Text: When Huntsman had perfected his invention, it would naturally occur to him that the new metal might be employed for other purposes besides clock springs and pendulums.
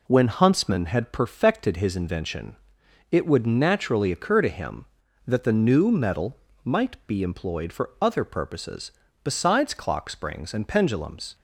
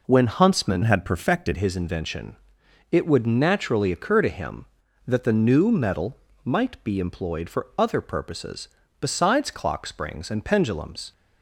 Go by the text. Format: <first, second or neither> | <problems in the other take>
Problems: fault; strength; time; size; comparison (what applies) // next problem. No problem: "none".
first | changes voice from "had" to "perfected"; from 0.8 to 1.5 s; 0.7 s long // pauses between "metal" and "might"; slight; at 6.1 s; 0.28 s long; slight in the first // pauses between "purposes" and "besides"; slight; at 8.6 s; 0.32 s long; slight in the first